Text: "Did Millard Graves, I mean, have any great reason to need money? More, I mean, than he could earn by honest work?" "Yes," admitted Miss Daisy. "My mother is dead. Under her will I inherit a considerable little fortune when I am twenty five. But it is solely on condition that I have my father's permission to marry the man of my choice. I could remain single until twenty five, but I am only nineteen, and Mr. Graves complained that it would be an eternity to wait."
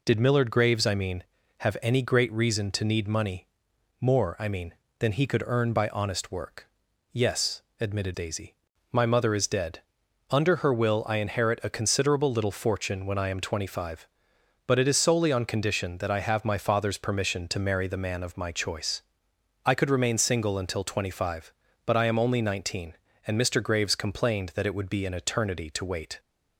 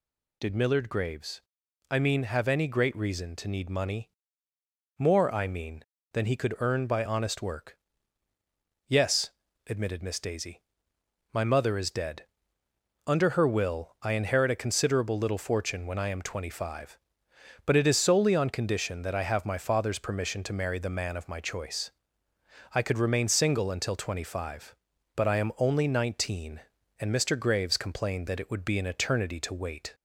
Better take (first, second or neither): second